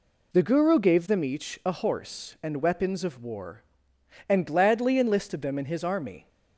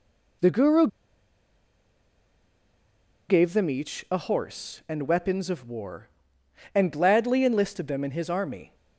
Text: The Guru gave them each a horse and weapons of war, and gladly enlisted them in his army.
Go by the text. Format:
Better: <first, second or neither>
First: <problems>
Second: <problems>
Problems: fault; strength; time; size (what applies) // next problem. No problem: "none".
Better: first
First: none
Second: pauses between "Guru" and "gave"; strong; at 0.8 s; 2.4 s long